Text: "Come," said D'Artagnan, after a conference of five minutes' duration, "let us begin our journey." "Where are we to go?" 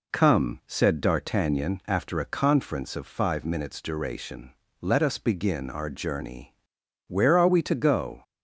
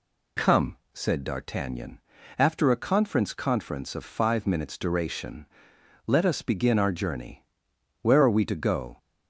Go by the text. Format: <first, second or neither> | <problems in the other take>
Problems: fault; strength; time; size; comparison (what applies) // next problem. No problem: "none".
first | says "conference" twice; at 3.3 s